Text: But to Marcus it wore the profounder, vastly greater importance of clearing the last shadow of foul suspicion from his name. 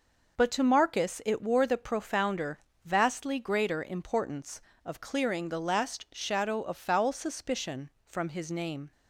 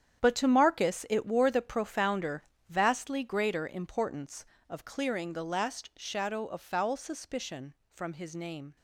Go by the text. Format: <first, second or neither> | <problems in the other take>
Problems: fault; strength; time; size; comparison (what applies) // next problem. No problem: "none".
first | gets quieter; strong; throughout; 12.5 dB